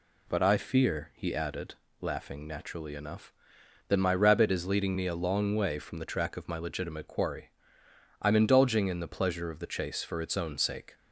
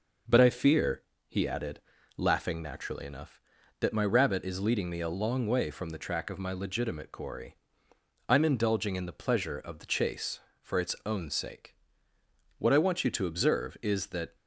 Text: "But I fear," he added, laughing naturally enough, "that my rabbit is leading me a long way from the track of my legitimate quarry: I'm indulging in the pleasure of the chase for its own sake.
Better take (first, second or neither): first